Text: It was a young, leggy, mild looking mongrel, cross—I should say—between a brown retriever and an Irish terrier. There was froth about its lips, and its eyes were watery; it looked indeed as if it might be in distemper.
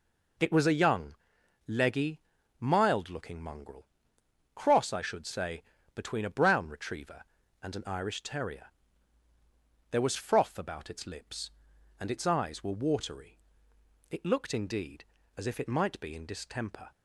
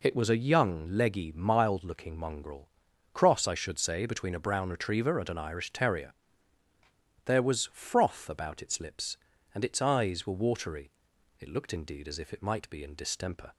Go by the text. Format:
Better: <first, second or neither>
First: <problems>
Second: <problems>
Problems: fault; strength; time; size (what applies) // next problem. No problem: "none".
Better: neither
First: none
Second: none